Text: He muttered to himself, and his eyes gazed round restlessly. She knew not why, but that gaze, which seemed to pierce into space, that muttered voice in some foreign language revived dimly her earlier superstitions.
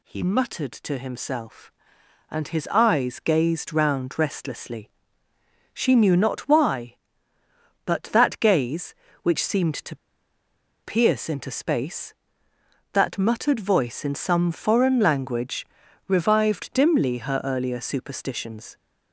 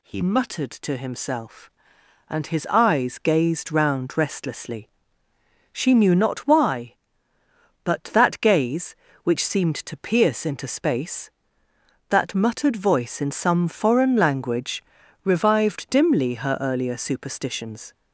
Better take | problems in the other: second | pauses between "to" and "pierce"; noticeable; at 9.9 s; 0.86 s long // pauses between "language" and "revived"; at 15.6 s; 0.40 s long; also in the second

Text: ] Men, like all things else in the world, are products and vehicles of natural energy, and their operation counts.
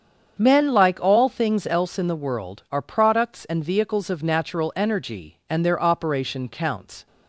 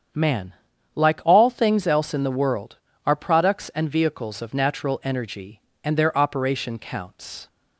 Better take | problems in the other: first | starts louder than the rest; strong; until 1.5 s; 8 dB; strong in the first // says "Man" for "Men"; at 0.1 s

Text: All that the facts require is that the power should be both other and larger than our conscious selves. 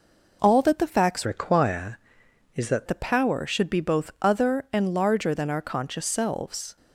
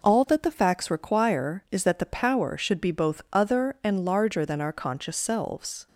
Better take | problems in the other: second | changes voice from "require" to "that"; from 1.2 to 2.8 s; 1.6 s long

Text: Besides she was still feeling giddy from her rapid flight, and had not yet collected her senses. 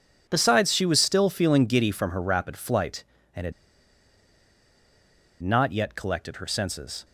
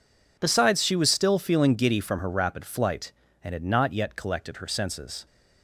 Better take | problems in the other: second | pauses between "had" and "not"; strong; at 3.5 s; 1.9 s long

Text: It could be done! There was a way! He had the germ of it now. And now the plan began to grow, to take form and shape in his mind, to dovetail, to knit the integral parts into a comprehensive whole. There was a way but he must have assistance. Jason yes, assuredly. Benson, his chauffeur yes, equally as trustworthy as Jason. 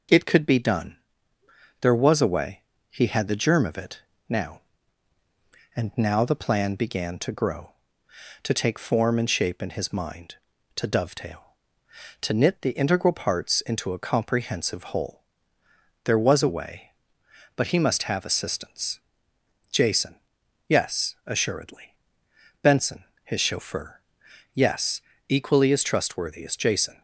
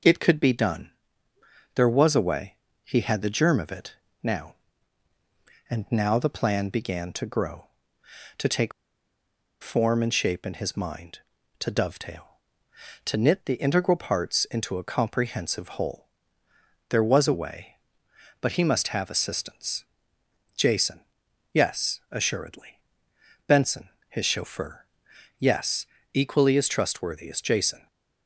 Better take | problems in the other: first | pauses between "it" and "now"; slight; at 3.9 s; 0.26 s long; slight in the first // pauses between "take" and "form"; noticeable; at 8.7 s; 0.91 s long // pauses between "Jason" and "yes"; noticeable; at 21.0 s; 0.54 s long; noticeable in the first // pauses between "chauffeur" and "yes"; noticeable; at 24.8 s; 0.54 s long; noticeable in the first

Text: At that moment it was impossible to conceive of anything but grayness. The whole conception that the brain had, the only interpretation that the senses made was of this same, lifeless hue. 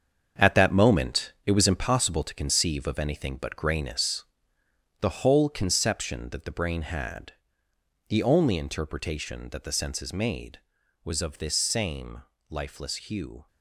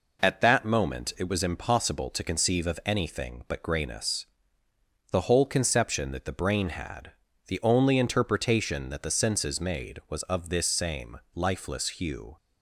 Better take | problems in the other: second | gets quieter; strong; throughout; 8.5 dB

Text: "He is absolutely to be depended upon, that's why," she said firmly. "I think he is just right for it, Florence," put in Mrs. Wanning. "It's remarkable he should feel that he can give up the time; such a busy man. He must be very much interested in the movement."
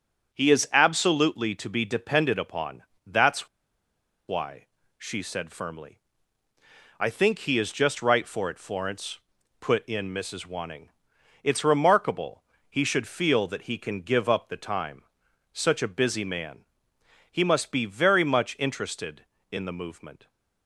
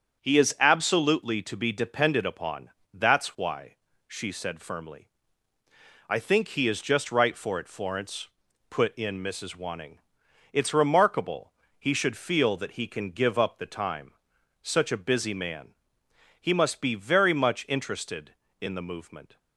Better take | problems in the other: second | starts louder than the rest; until 1.3 s; 7 dB; also in the second // pauses between "that's" and "why"; noticeable; at 3.4 s; 0.81 s long // pauses between "remarkable" and "he"; slight; at 12.4 s; 0.24 s long; slight in the second

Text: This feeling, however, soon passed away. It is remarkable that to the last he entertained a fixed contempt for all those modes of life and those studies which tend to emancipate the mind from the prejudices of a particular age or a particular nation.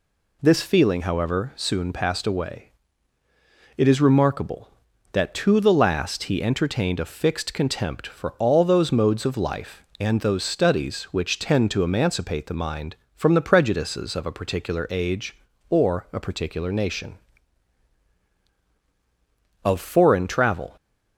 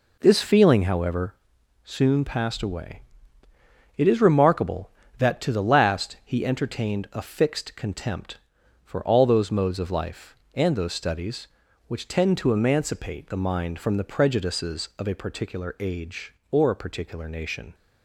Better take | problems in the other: second | goes on to say "Of foreign travel"; noticeable; from 19.6 s on; 1.1 s long

